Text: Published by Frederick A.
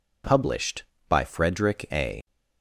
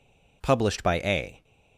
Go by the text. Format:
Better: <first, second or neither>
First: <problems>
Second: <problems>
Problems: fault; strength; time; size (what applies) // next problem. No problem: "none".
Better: first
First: none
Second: skips "Frederick"; at 1.0 s